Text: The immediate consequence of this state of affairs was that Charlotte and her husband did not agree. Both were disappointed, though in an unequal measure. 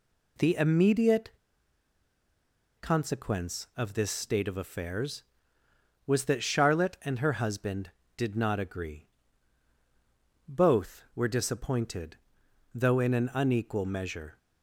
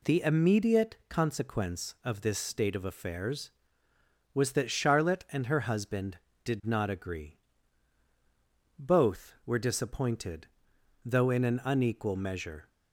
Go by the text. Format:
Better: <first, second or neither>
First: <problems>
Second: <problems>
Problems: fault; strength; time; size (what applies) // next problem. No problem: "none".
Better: second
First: pauses between "immediate" and "consequence"; strong; at 1.3 s; 1.4 s long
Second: none